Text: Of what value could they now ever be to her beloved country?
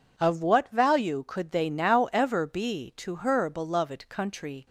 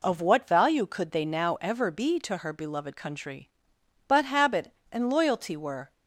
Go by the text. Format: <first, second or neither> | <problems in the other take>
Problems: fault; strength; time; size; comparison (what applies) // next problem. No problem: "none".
first | goes on to say "But habit and loyalty were"; strong; from 4.0 s on; 1.8 s long